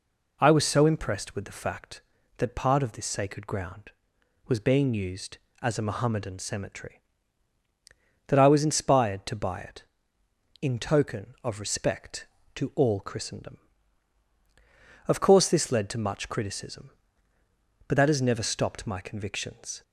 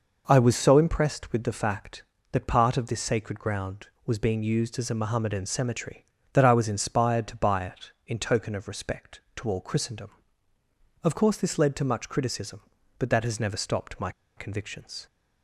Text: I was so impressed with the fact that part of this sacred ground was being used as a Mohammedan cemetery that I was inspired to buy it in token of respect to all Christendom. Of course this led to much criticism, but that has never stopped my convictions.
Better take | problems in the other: first | pauses between "my" and "convictions"; slight; at 14.0 s; 0.26 s long

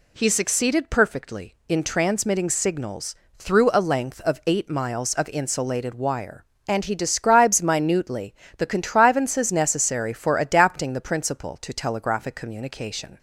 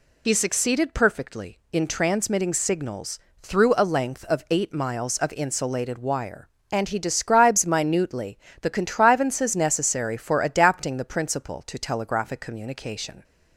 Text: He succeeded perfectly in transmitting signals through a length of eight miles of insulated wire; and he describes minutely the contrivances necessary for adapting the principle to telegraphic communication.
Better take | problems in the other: first | loses the start of "He"; at 0.2 s; 50 ms // pauses between "signals" and "through"; slight; at 3.1 s; 0.22 s long; slight in the first // pauses between "minutely" and "the"; slight; at 8.3 s; 0.22 s long; slight in the first

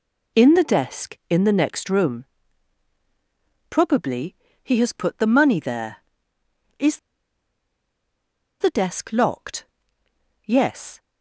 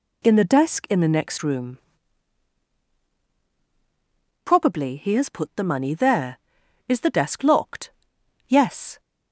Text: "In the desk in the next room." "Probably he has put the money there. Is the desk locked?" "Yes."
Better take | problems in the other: second | pauses between "Probably" and "he"; slight; at 4.3 s; 0.30 s long // pauses between "Is" and "the"; strong; at 6.9 s; 1.6 s long

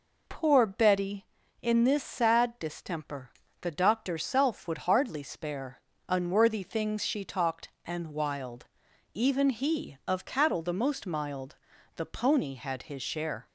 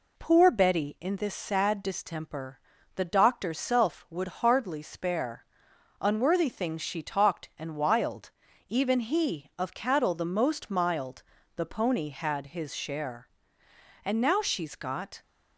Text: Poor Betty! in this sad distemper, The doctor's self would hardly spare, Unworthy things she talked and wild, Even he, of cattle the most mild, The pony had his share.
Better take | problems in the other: first | goes on to say "And now she's got"; noticeable; from 14.0 s on; 1.1 s long

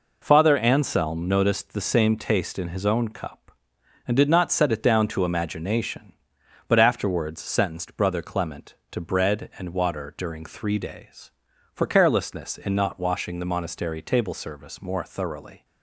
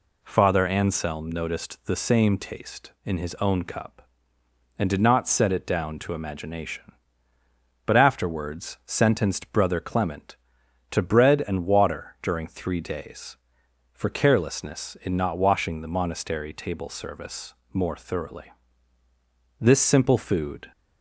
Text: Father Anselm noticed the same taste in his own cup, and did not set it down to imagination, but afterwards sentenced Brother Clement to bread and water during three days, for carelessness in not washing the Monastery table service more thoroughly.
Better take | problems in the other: first | pauses between "service" and "more"; slight; at 17.5 s; 0.20 s long // goes on to say "This simple food"; noticeable; from 19.5 s on; 1.1 s long

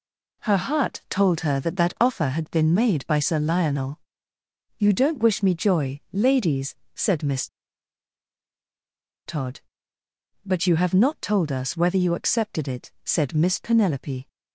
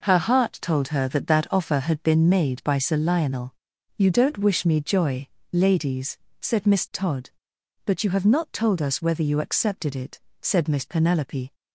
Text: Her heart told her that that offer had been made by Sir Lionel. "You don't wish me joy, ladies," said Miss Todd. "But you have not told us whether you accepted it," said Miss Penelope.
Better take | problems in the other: second | pauses between "Miss" and "Todd"; strong; at 7.4 s; 1.7 s long

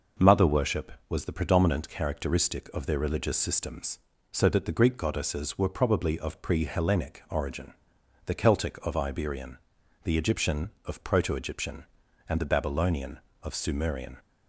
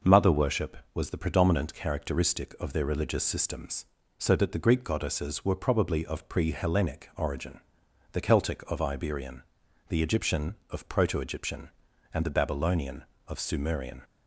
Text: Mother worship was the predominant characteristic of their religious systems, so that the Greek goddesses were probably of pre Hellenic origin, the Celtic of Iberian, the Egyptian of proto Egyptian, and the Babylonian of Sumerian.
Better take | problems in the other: neither | none

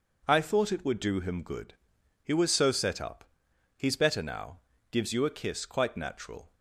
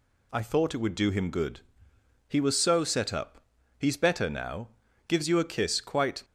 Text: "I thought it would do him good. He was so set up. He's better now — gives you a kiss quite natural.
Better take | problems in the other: first | stops before "natural"; at 6.2 s

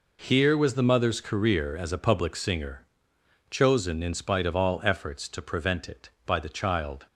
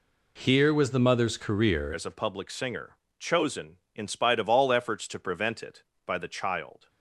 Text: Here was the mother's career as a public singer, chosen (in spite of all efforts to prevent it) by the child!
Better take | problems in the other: first | changes voice at "as"; from 1.9 s on; 4.9 s long

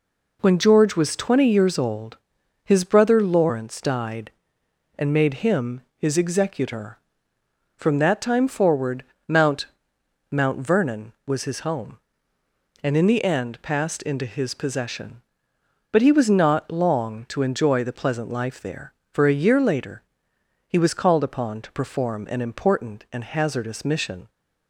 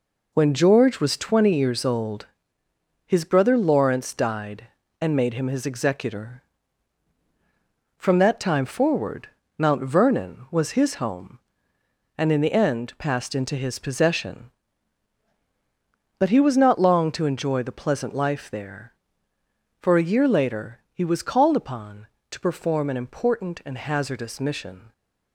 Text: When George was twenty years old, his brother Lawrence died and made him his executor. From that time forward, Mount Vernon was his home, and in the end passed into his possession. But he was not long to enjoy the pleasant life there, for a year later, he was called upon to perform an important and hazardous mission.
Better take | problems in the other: second | pauses between "him" and "his"; slight; at 5.8 s; 0.15 s long // says "Mount" twice; at 10.3 s

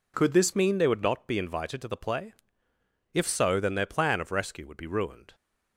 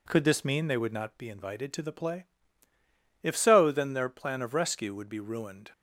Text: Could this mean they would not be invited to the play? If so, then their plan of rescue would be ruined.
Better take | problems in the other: second | changes voice at "mean"; from 0.5 s on; 4.8 s long

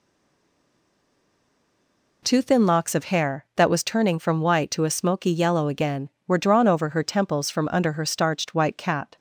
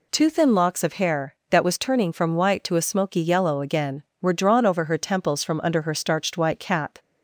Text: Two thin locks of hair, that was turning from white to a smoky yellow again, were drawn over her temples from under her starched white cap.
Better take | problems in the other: second | stays silent before the first word; until 2.2 s; 2.2 s long

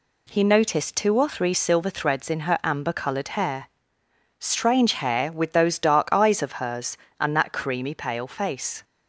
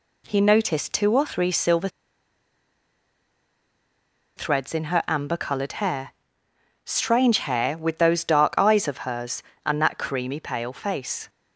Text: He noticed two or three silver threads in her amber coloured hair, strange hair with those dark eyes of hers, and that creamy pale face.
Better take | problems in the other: first | pauses between "silver" and "threads"; strong; at 1.8 s; 2.4 s long

